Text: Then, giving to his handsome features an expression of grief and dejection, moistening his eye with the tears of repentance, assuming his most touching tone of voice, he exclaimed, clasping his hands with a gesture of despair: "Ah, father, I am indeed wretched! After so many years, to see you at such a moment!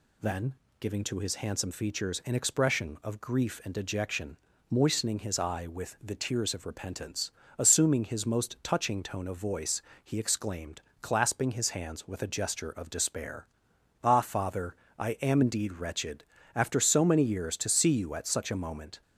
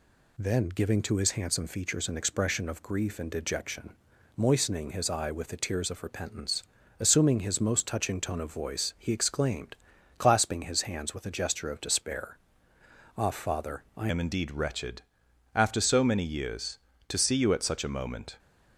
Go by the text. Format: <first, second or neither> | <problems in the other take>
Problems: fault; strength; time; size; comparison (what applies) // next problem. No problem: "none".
first | changes voice at "am"; from 14.0 s on; 4.3 s long